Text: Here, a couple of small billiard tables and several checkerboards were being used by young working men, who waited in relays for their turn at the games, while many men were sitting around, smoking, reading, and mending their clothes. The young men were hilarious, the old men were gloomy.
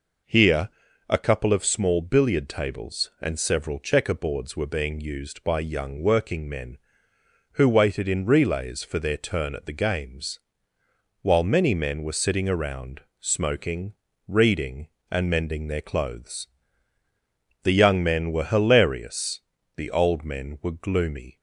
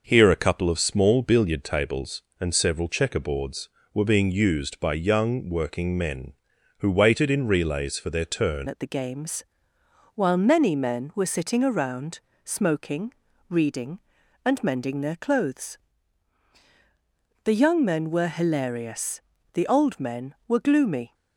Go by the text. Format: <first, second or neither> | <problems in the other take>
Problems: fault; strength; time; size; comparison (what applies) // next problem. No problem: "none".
first | changes voice at "at"; from 8.6 s on; 12.5 s long